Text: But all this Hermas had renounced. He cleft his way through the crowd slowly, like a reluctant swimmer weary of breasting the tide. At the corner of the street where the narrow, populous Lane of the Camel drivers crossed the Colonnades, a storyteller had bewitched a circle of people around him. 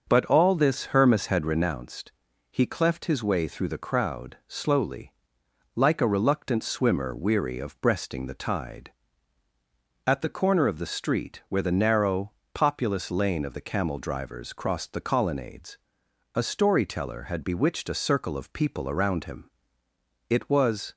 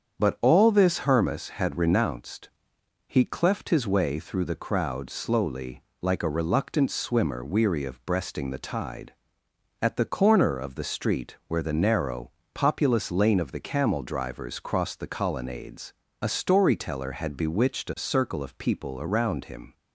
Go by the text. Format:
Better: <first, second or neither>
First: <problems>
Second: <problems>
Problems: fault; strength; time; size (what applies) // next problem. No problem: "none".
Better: second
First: starts louder than the rest; until 1.1 s; 6.5 dB // goes on to say "It was"; noticeable; from 20.2 s on; 0.66 s long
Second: starts louder than the rest; strong; until 1.2 s; 7.5 dB